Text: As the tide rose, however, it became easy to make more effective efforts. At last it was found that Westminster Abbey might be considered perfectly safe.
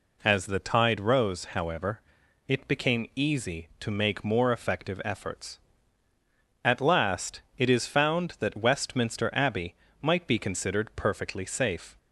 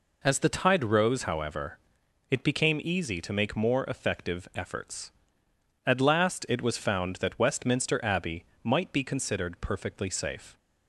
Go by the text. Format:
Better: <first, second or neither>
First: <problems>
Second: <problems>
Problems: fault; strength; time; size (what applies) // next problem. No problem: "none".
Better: second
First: pauses between "last" and "it"; slight; at 7.4 s; 0.16 s long // says "is" for "was"; at 7.6 s // pauses between "Abbey" and "might"; slight; at 9.7 s; 0.26 s long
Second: pauses between "Abbey" and "might"; slight; at 8.4 s; 0.20 s long